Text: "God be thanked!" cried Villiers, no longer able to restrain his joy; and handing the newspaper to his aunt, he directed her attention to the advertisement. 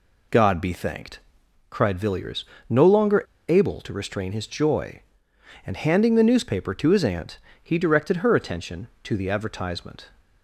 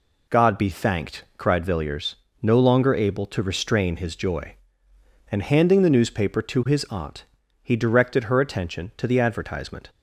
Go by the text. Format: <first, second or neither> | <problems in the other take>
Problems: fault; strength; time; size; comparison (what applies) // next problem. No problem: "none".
second | pauses between "longer" and "able"; slight; at 3.2 s; 0.25 s long